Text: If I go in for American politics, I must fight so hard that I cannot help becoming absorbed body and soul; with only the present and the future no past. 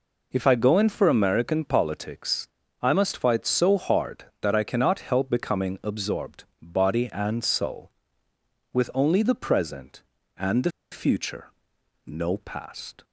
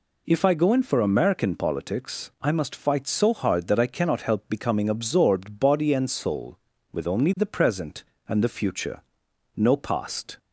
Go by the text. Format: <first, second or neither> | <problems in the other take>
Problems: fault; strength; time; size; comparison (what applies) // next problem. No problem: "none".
second | pauses between "absorbed" and "body"; slight; at 6.4 s; 0.16 s long // pauses between "the" and "future"; slight; at 10.7 s; 0.20 s long // pauses between "future" and "no"; noticeable; at 11.4 s; 0.60 s long; noticeable in the second